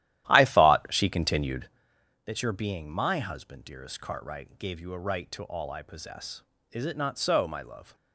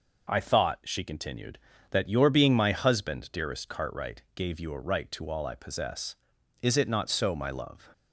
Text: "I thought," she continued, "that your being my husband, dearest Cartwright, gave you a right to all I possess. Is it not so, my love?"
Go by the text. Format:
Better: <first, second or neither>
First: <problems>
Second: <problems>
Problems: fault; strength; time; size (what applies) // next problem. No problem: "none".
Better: second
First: starts louder than the rest; strong; until 1.9 s; 13.5 dB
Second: none